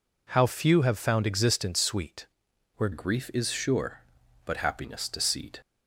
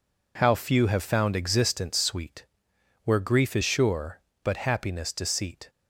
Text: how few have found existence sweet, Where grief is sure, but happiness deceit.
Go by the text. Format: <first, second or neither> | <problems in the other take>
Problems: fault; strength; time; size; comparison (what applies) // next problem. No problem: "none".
second | changes voice at "grief"; from 2.9 s on; 2.6 s long